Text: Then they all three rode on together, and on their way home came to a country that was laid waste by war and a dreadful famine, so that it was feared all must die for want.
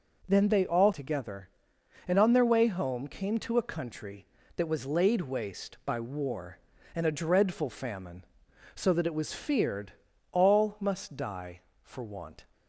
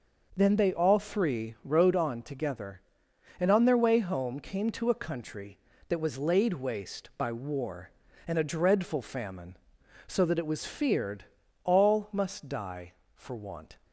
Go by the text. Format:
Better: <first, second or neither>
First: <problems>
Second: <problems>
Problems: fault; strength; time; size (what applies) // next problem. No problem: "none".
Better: second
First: skips "three rode on"; at 0.9 s // pauses between "feared" and "all"; at 9.9 s; 0.40 s long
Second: pauses between "feared" and "all"; at 11.2 s; 0.40 s long